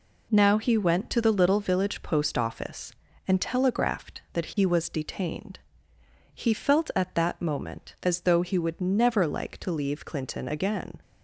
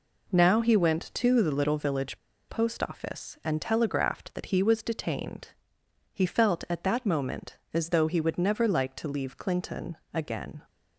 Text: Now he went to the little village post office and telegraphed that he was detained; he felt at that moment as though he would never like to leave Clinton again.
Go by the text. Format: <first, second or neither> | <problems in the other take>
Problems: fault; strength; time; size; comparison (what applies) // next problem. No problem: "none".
first | pauses between "village" and "post"; slight; at 2.1 s; 0.31 s long // pauses between "Clinton" and "again"; slight; at 9.9 s; 0.18 s long